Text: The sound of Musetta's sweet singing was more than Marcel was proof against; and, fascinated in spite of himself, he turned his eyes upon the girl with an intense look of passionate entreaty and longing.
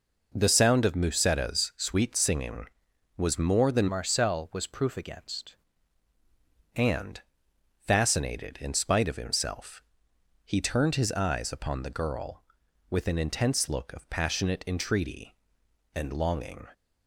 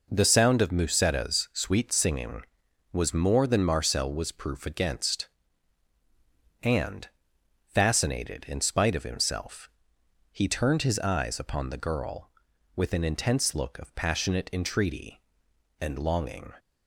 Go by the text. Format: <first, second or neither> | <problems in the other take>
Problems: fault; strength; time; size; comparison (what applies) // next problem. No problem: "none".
second | changes voice from "Marcel" to "against"; from 3.8 to 5.5 s; 1.7 s long